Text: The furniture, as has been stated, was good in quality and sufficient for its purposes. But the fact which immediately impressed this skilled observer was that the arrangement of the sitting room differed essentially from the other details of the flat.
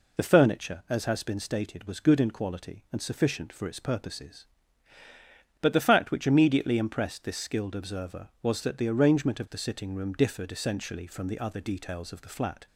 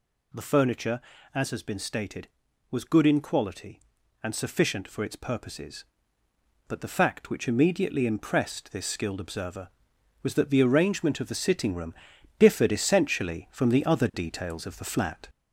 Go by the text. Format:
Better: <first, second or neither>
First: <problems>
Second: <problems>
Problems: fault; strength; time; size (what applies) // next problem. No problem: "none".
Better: first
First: none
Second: gets louder; throughout; 3.5 dB // pauses between "room" and "differed"; at 11.9 s; 0.44 s long